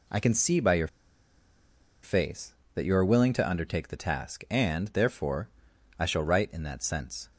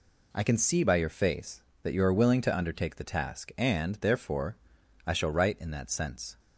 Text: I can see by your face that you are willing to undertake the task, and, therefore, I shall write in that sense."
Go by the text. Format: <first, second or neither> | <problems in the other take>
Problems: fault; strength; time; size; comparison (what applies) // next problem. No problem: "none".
second | pauses between "your" and "face"; at 0.8 s; 1.1 s long